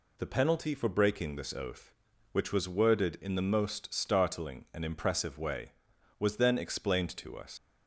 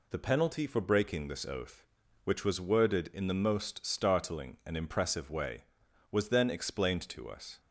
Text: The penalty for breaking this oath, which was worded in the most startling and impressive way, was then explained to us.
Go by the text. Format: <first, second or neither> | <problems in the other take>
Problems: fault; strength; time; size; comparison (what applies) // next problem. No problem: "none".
second | leaves "us" unfinished; at 7.5 s; 100 ms